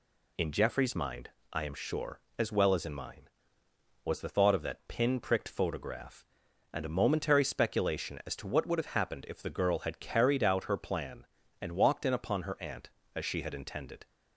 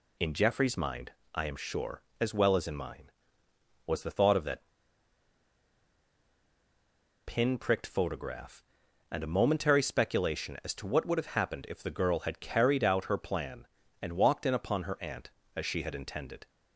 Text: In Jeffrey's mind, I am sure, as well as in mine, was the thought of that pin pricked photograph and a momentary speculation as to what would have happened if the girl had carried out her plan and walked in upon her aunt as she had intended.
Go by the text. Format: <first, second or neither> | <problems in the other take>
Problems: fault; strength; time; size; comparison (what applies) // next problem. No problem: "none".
first | pauses between "that" and "pin"; strong; at 4.6 s; 2.6 s long